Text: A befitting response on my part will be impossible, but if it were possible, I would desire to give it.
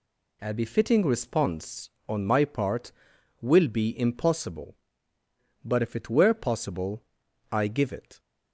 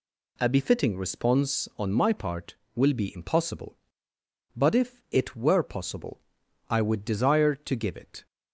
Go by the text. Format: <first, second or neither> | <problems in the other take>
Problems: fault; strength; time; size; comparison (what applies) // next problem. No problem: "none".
second | skips "would desire to"; at 7.6 s